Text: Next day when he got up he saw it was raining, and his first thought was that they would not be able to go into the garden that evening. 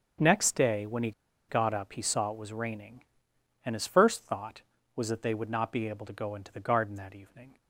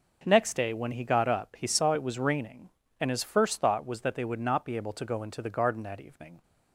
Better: second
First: starts louder than the rest; strong; until 1.5 s; 7 dB // pauses between "he" and "got"; at 1.1 s; 0.37 s long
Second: none

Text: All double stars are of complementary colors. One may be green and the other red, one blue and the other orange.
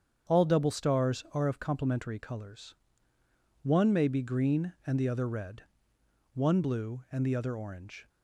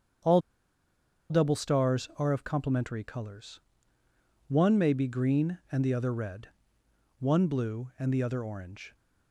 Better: first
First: starts louder than the rest; strong; until 1.3 s; 7.5 dB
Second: starts louder than the rest; strong; until 2.2 s; 8 dB // pauses between "All" and "double"; noticeable; at 0.4 s; 0.89 s long

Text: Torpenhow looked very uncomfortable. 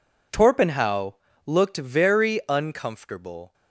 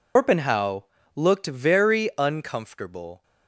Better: first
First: pauses between "Torpenhow" and "looked"; slight; at 1.1 s; 0.30 s long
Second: loses the start of "Torpenhow"; at 0.1 s; 150 ms // pauses between "Torpenhow" and "looked"; slight; at 0.8 s; 0.30 s long

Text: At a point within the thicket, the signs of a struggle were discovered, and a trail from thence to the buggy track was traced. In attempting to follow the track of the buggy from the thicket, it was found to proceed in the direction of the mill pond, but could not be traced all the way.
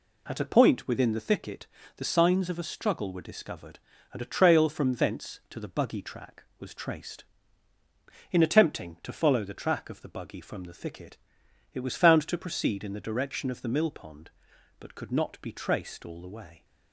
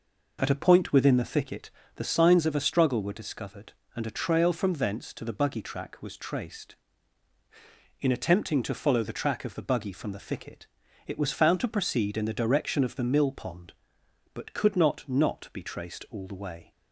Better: first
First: none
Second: says "not" twice; at 15.0 s

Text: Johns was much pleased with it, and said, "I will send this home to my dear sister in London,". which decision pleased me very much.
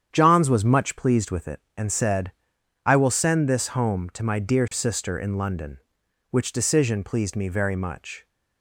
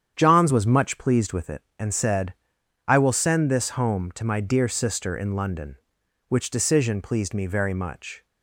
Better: neither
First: starts louder than the rest; strong; until 1.1 s; 8.5 dB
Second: starts louder than the rest; strong; until 1.1 s; 8.5 dB

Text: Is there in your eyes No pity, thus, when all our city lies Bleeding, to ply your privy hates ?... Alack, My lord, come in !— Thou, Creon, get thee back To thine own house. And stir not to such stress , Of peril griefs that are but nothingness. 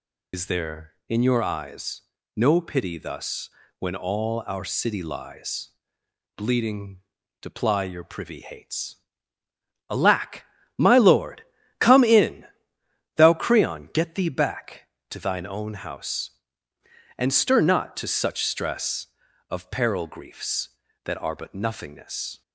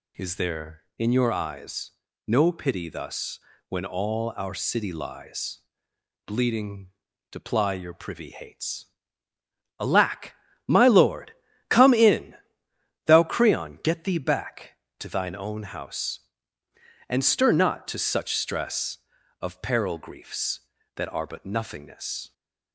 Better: second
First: loses the start of "Is"; at 0.3 s; 65 ms // pauses between "eyes" and "No"; slight; at 2.0 s; 0.34 s long // pauses between "lies" and "Bleeding"; noticeable; at 5.6 s; 0.68 s long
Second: pauses between "eyes" and "No"; slight; at 1.9 s; 0.36 s long // pauses between "lies" and "Bleeding"; noticeable; at 5.5 s; 0.68 s long

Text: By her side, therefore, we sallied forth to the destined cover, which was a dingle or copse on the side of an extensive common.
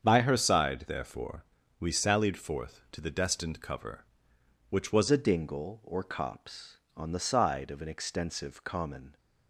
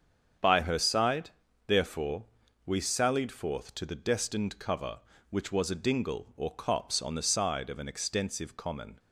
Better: second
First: starts louder than the rest; strong; until 1.0 s; 7.5 dB // changes voice at "a"; from 5.1 s on; 4.0 s long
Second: starts louder than the rest; strong; until 1.7 s; 7.5 dB

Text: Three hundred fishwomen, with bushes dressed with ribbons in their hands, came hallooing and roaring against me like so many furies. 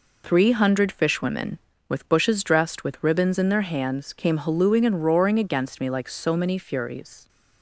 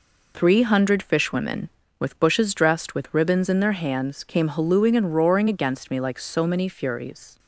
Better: neither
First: none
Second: none

